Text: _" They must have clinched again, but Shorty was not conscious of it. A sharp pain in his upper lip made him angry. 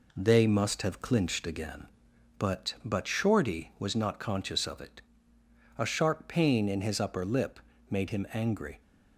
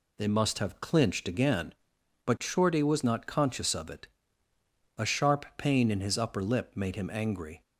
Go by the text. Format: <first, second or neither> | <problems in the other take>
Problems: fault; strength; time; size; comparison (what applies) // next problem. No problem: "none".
second | says "but" twice; at 2.8 s // pauses between "lip" and "made"; slight; at 7.5 s; 0.30 s long